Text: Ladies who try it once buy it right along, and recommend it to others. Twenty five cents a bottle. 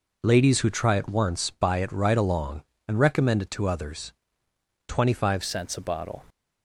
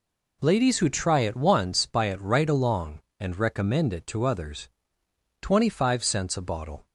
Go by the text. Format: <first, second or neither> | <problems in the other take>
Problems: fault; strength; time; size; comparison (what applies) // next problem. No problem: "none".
second | changes voice at "cents"; from 5.4 s on; 0.8 s long